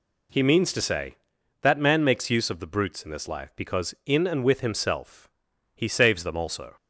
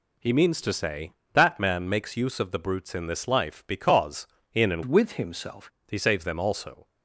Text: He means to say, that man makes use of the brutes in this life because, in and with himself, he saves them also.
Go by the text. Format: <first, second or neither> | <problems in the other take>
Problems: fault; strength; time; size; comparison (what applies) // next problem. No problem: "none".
first | changes voice from "with" to "himself"; from 4.8 to 5.7 s; 0.9 s long